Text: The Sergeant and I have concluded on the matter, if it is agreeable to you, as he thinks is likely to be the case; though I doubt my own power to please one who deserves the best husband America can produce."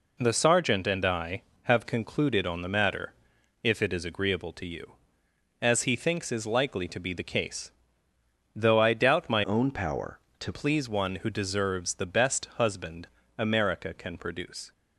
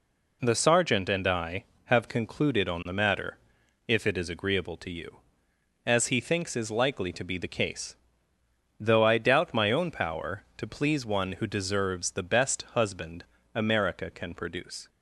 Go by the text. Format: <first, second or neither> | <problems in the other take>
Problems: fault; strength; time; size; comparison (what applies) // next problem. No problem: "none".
second | changes voice from "own" to "to"; from 9.4 to 10.5 s; 1.1 s long // pauses between "husband" and "America"; slight; at 13.0 s; 0.32 s long; slight in the second